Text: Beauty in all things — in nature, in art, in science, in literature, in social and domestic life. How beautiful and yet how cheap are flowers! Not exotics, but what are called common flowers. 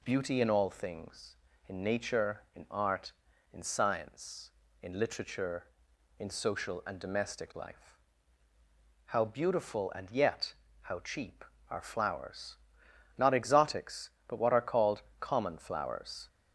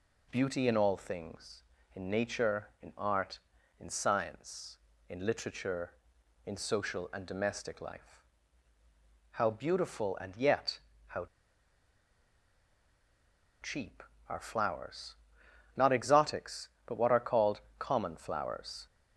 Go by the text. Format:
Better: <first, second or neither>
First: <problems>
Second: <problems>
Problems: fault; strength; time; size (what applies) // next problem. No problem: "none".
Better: first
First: pauses between "yet" and "how"; slight; at 10.5 s; 0.26 s long // pauses between "called" and "common"; slight; at 15.0 s; 0.18 s long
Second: pauses between "yet" and "how"; slight; at 10.8 s; 0.26 s long // pauses between "how" and "cheap"; strong; at 11.2 s; 2.3 s long // pauses between "called" and "common"; slight; at 17.6 s; 0.18 s long